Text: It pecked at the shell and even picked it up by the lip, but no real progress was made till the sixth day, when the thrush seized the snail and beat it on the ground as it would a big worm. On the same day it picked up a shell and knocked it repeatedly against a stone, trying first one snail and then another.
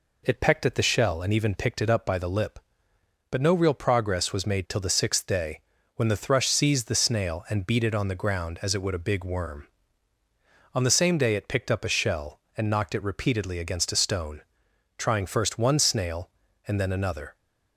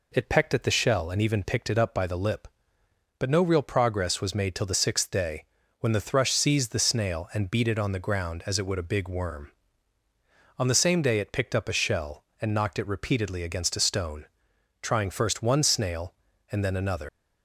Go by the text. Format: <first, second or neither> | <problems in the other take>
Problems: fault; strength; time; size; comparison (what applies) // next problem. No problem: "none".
first | leaves "another" unfinished; at 17.0 s; 125 ms